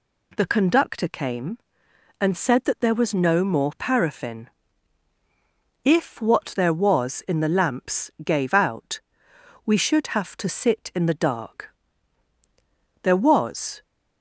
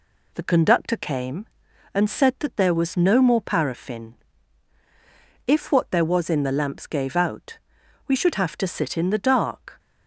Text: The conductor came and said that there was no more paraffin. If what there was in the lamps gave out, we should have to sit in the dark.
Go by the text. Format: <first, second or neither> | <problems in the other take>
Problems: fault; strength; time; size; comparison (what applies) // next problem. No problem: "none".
second | goes on to say "There was"; noticeable; from 13.0 s on; 0.80 s long